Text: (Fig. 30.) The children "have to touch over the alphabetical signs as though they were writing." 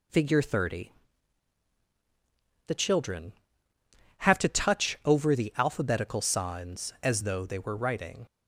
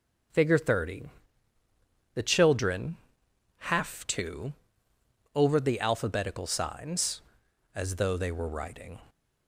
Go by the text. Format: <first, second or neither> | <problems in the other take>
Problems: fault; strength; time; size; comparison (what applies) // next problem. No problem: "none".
first | skips "touch"; at 4.9 s